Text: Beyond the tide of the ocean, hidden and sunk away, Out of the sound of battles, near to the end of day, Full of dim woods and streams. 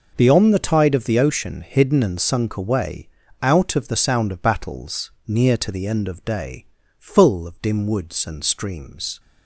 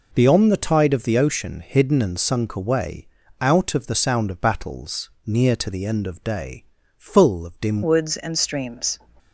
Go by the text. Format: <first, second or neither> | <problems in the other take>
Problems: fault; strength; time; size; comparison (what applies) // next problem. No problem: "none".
first | changes voice at "woods"; from 7.8 s on; 1.2 s long